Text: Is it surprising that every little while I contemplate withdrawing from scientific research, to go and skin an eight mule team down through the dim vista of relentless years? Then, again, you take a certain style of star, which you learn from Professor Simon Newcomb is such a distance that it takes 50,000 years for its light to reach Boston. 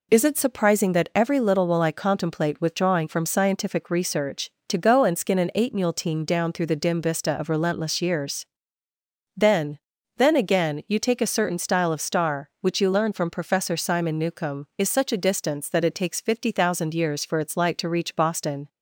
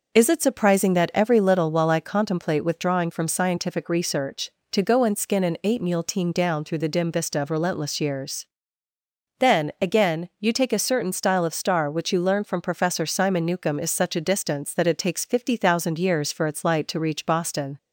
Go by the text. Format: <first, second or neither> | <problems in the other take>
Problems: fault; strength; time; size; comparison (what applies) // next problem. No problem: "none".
second | says "Then" twice; at 10.1 s